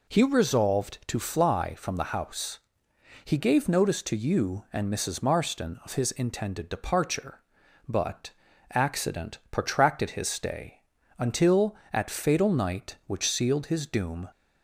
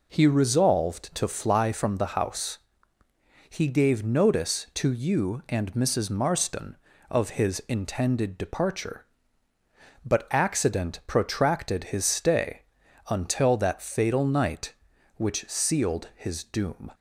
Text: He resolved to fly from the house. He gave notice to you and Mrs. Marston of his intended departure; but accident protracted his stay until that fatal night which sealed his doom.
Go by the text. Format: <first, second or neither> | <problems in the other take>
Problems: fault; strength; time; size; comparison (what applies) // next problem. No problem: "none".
second | pauses between "but" and "accident"; at 8.3 s; 0.40 s long // pauses between "stay" and "until"; at 10.8 s; 0.38 s long; noticeable in the second // says "at" for "that"; at 11.9 s